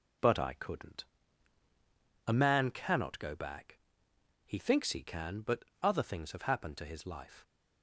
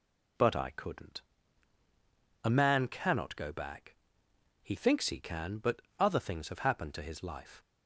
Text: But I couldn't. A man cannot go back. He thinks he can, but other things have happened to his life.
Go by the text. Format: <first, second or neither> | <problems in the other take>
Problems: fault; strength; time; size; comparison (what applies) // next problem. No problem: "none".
second | gets quieter; throughout; 6.5 dB // pauses between "but" and "other"; slight; at 5.6 s; 0.18 s long; slight in the second